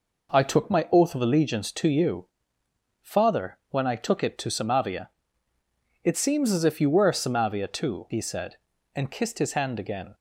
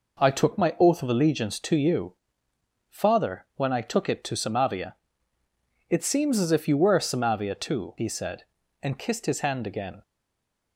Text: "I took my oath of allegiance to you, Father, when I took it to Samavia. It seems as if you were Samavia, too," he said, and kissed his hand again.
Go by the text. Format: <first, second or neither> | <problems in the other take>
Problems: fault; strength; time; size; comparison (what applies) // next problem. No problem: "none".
first | stays silent after the last word; slight; from 10.0 s on; 0.7 s long